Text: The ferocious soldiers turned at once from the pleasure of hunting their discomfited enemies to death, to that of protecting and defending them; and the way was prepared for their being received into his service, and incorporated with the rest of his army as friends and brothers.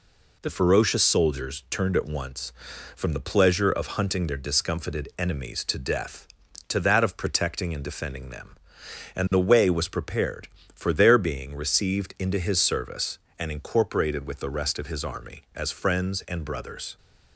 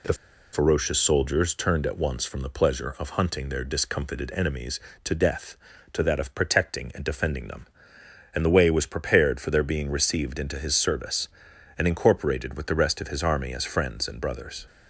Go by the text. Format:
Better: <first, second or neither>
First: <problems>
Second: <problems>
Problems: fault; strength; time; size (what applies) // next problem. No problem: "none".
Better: first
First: none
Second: pauses between "The" and "ferocious"; at 0.1 s; 0.39 s long